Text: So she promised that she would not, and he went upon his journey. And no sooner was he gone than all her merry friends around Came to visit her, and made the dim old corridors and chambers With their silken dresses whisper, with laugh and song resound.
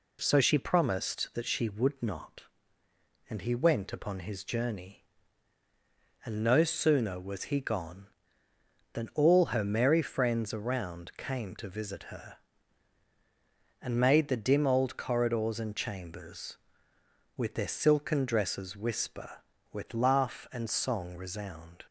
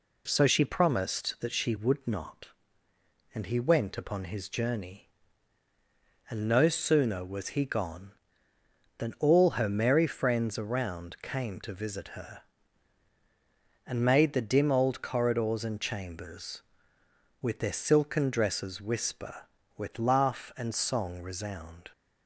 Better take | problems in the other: neither | none

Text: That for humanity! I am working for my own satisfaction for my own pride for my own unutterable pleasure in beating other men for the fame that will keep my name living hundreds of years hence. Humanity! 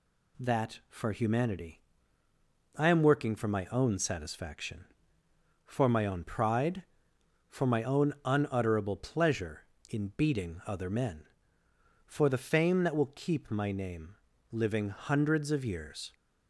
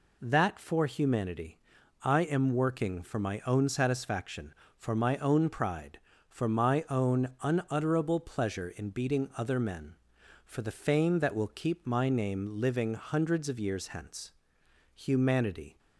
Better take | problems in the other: second | pauses between "name" and "living"; slight; at 14.1 s; 0.34 s long // stops before "hence Humanity"; at 16.1 s

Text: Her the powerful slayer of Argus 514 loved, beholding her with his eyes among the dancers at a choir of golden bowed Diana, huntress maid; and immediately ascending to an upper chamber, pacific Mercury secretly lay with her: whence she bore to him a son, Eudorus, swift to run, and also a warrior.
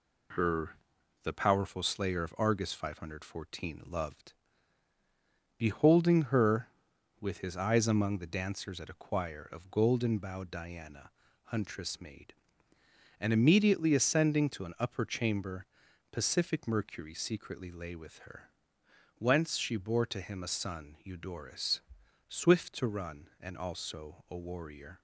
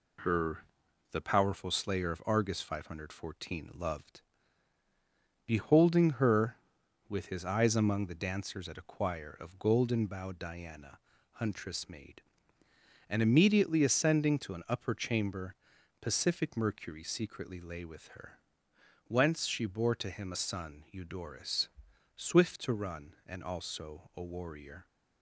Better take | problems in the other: neither | pauses between "Her" and "the"; noticeable; the same in both

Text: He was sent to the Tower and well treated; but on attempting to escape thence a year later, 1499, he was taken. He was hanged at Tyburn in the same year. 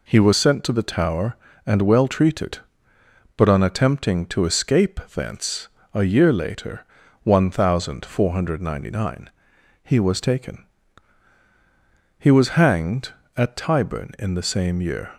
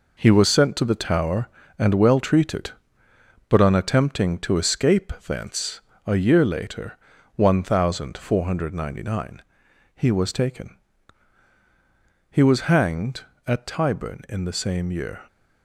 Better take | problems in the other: first | gets quieter; strong; throughout; 8 dB // pauses between "thence" and "a"; slight; at 5.7 s; 0.28 s long; slight in the first

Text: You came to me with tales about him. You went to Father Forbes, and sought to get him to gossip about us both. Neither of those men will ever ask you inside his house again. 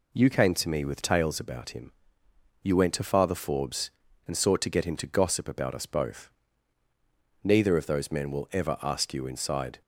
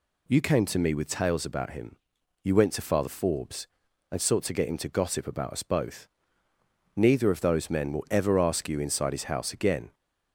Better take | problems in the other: second | stops before "his house again"; at 9.8 s

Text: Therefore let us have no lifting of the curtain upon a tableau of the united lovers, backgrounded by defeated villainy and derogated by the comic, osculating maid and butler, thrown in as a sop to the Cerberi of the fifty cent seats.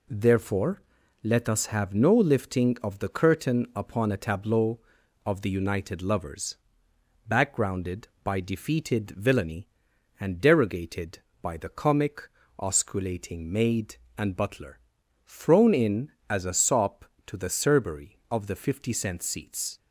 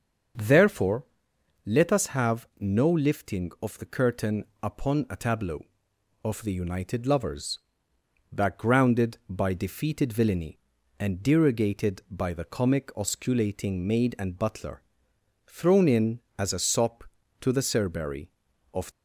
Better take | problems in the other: first | starts louder than the rest; until 1.9 s; 7 dB // pauses between "Therefore" and "let"; noticeable; at 1.0 s; 0.60 s long; also in the first // pauses between "curtain" and "upon"; slight; at 4.4 s; 0.18 s long // stops before "the fifty cent seats"; at 18.9 s

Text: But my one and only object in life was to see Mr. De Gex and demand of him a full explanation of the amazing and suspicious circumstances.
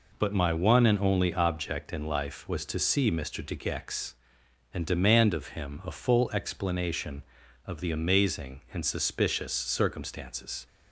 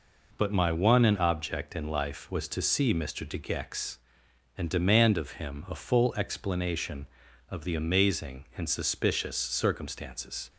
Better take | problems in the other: first | skips "only"; at 1.1 s

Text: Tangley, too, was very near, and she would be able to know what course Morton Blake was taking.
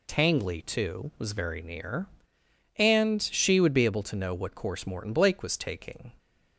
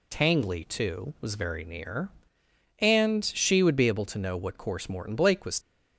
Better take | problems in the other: first | stops before "taking"; at 5.6 s

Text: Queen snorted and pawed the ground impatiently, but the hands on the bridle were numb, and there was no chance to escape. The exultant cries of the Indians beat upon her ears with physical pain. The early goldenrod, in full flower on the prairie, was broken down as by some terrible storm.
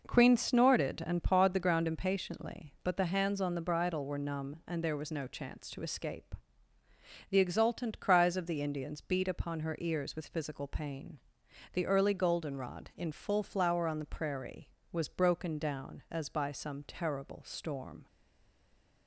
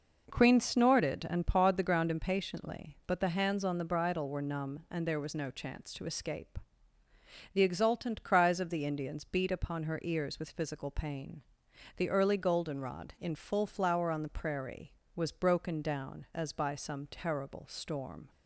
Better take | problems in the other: second | stays silent after the last word; from 18.0 s on; 1.0 s long

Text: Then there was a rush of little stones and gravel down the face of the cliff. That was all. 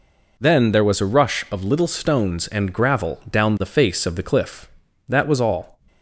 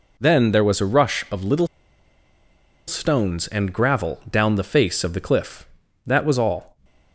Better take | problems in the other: first | pauses between "little" and "stones"; at 1.6 s; 1.2 s long

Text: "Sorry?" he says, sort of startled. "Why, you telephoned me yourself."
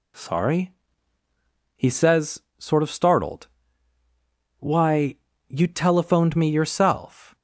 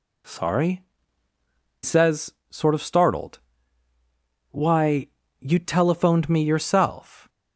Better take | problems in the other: first | skips "he"; at 1.3 s

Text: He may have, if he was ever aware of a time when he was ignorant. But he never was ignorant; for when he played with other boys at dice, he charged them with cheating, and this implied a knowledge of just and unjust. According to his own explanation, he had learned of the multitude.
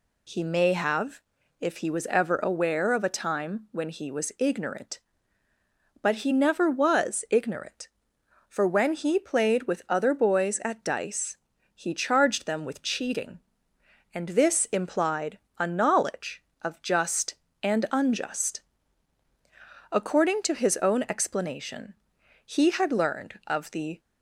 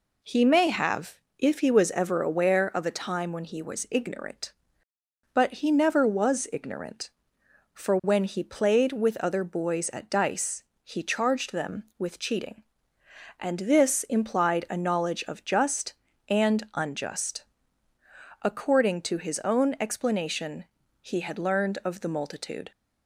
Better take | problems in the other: second | pauses between "implied" and "a"; slight; at 15.3 s; 0.22 s long // stops before "multitude"; at 23.9 s

